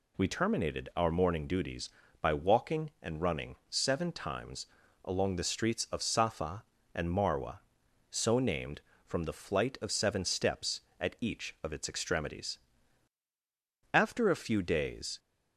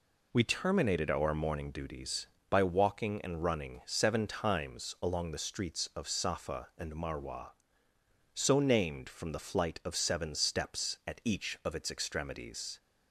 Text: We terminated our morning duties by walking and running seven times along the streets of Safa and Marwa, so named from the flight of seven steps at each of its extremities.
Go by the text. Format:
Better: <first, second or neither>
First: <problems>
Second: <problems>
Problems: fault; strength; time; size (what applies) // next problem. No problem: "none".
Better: second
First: pauses between "times" and "along"; at 4.6 s; 0.38 s long // goes on to say "After a few days"; noticeable; from 13.9 s on; 1.2 s long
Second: none